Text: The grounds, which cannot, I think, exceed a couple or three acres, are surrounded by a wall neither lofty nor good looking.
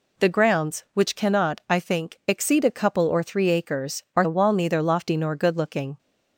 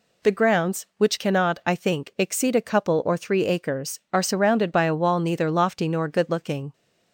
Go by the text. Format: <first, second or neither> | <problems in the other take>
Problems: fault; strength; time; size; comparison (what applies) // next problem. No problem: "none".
second | skips "surrounded by"; at 4.2 s